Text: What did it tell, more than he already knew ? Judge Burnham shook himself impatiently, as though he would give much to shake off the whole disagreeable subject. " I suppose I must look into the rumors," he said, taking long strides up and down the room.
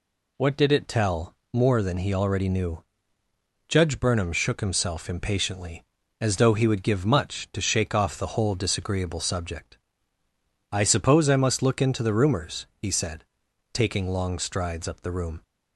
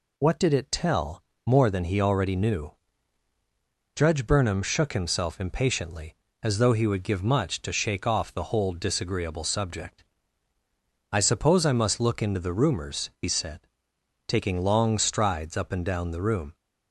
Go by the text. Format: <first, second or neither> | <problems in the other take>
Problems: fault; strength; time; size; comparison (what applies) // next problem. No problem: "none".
second | skips "and down"; at 15.0 s